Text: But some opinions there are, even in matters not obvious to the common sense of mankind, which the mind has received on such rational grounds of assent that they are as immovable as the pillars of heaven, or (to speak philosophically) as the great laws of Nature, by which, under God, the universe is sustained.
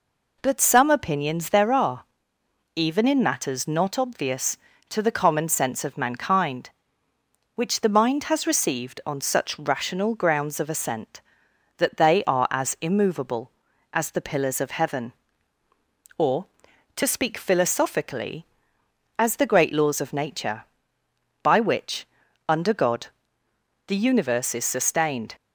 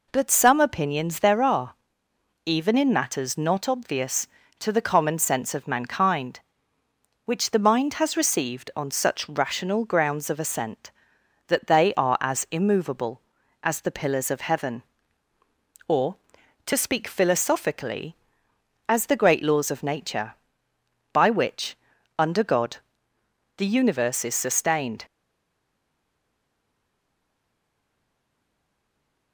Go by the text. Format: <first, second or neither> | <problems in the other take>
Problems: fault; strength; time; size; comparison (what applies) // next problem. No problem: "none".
first | stays silent after the last word; strong; from 25.0 s on; 4.3 s long